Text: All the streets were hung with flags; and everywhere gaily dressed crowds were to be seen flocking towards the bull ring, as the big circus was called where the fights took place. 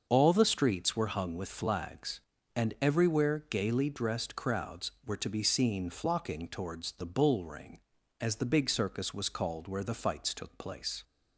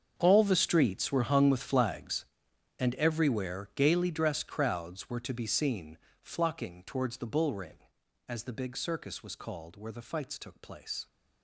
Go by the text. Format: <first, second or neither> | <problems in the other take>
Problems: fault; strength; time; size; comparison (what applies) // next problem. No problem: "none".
first | gets quieter; strong; throughout; 16 dB // starts louder than the rest; until 1.1 s; 7 dB; also in the first // pauses between "seen" and "flocking"; slight; at 5.9 s; 0.24 s long